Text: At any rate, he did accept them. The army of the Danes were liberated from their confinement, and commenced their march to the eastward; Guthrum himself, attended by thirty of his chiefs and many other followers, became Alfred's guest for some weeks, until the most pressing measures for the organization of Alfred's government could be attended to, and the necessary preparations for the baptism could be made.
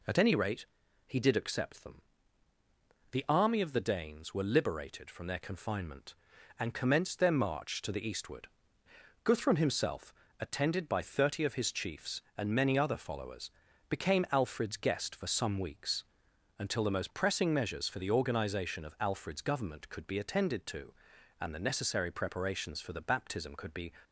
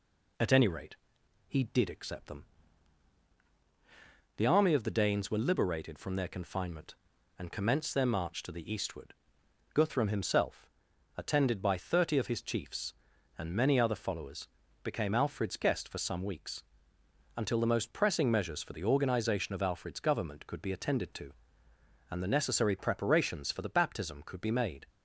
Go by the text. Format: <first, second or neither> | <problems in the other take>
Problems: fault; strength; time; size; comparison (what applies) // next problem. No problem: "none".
second | stops before "made"; at 24.0 s